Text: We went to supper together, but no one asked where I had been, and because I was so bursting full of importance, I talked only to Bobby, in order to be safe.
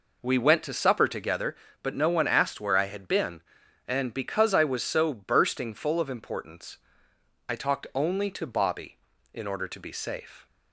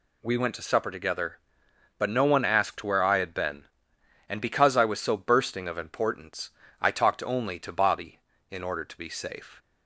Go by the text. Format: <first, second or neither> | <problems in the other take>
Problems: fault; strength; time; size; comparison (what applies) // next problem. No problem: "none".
first | skips "full"; at 5.6 s